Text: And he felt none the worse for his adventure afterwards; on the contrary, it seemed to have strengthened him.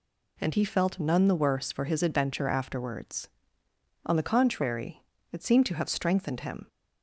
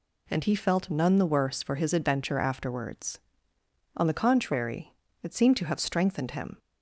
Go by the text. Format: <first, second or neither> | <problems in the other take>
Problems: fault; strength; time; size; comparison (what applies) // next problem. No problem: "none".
neither | none